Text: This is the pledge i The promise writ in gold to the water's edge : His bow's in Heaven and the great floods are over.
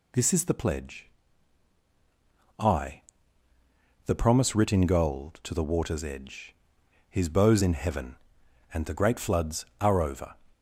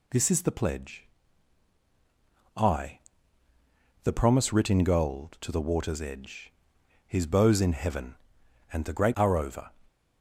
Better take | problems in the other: first | pauses between "pledge" and "i"; strong; at 1.0 s; 1.4 s long; strong in the first // pauses between "i" and "The"; at 2.9 s; 1.0 s long; also in the first // skips "floods"; at 9.1 s

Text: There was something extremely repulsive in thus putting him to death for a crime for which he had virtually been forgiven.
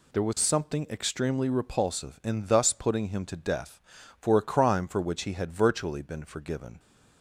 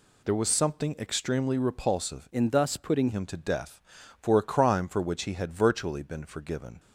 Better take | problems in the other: first | changes voice from "in" to "putting"; from 2.3 to 3.0 s; 0.7 s long

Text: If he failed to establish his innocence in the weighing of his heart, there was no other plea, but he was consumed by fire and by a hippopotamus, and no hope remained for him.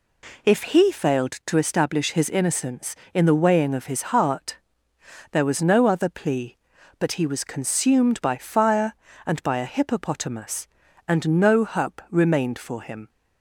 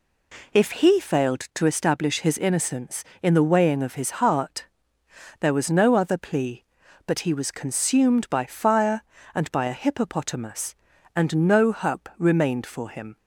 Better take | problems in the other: neither | none

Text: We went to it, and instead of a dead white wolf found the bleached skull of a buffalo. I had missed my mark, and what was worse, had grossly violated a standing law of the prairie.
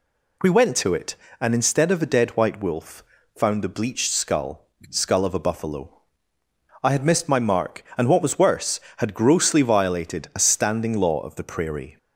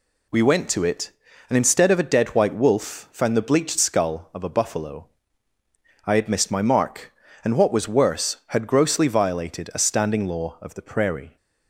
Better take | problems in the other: second | pauses between "wolf" and "found"; slight; at 3.0 s; 0.34 s long // says "skull" twice; at 4.9 s

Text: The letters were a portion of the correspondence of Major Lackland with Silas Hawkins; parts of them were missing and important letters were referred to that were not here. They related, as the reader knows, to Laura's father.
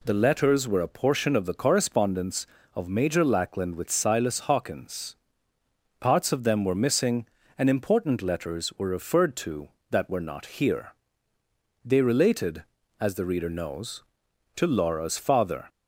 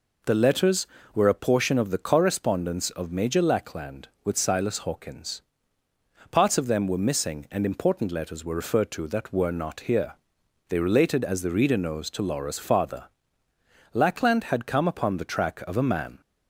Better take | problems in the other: first | goes on to say "Lackland had come upon the track of a man"; strong; from 13.9 s on; 2.2 s long

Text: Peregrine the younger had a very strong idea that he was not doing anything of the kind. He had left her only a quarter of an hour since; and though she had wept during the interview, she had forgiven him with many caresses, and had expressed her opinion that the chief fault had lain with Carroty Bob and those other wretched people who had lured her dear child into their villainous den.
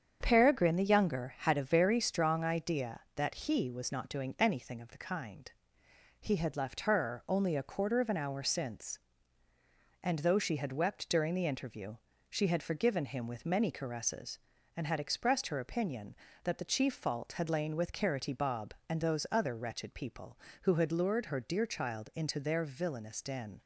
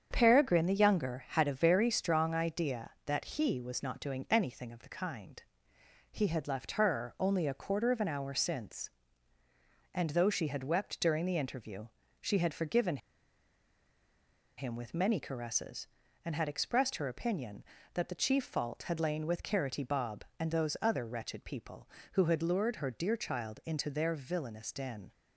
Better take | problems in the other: first | starts louder than the rest; strong; until 1.1 s; 8 dB; strong in the first // pauses between "forgiven" and "him"; strong; at 12.9 s; 1.5 s long

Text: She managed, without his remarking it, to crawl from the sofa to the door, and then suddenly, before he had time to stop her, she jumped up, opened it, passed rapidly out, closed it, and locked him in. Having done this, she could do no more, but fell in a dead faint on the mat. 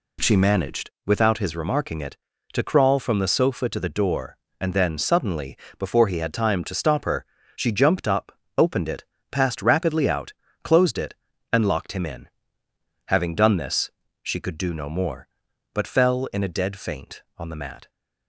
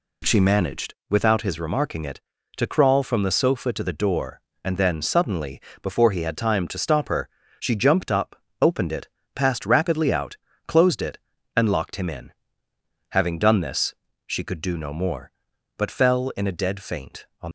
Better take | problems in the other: first | stops before "the mat"; at 17.4 s

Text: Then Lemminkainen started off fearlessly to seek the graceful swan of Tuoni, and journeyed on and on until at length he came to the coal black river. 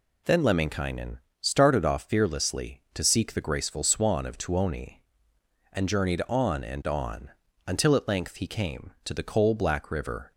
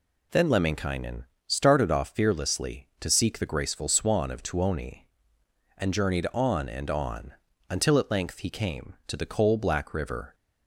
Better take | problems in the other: neither | pauses between "Lemminkainen" and "started"; slight; the same in both // pauses between "on" and "until"; slight; the same in both

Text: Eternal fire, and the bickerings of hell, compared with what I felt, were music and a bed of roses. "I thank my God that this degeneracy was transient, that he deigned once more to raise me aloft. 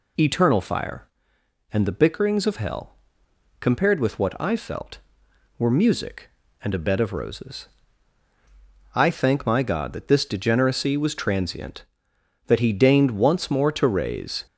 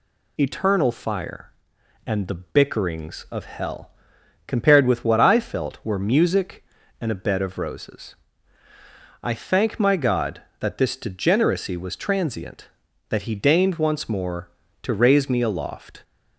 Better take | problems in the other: second | stops before "me aloft"; at 14.4 s

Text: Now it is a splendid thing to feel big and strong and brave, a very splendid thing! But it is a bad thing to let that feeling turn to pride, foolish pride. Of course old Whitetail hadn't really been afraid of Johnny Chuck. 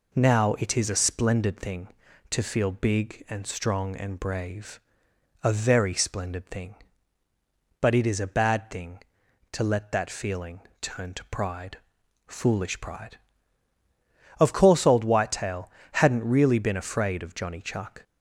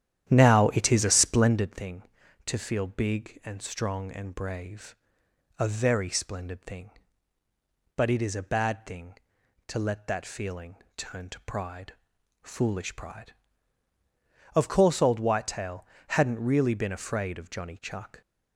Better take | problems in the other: first | starts louder than the rest; strong; until 1.7 s; 11 dB // pauses between "feeling" and "turn"; slight; at 10.7 s; 0.22 s long; slight in the first // pauses between "Whitetail" and "hadn't"; slight; at 15.8 s; 0.22 s long; slight in the first

